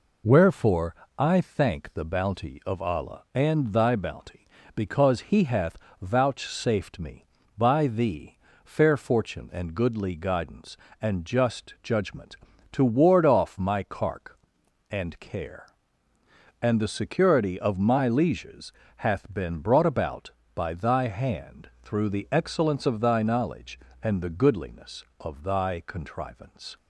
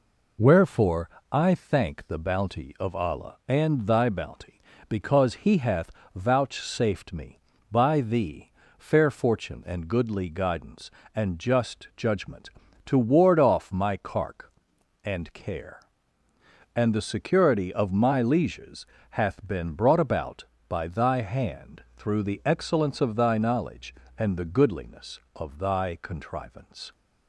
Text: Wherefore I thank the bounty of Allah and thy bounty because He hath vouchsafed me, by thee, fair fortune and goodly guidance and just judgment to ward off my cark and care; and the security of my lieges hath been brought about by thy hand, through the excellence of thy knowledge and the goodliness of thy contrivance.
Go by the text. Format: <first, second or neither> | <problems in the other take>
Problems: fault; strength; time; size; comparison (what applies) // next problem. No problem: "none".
neither | pauses between "Wherefore" and "I"; slight; the same in both // pauses between "hath" and "vouchsafed"; slight; the same in both // pauses between "lieges" and "hath"; slight; the same in both